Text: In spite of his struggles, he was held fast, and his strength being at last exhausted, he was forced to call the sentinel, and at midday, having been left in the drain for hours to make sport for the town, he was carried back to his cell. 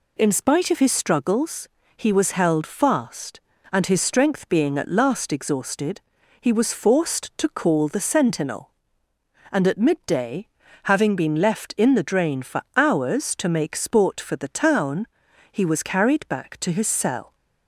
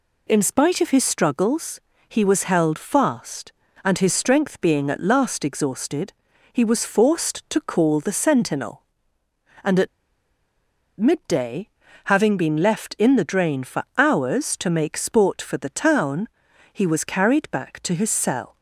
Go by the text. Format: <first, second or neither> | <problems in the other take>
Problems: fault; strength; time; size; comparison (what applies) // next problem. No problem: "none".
first | pauses between "at" and "midday"; at 9.8 s; 1.1 s long // pauses between "for" and "hours"; slight; at 13.8 s; 0.16 s long; slight in the first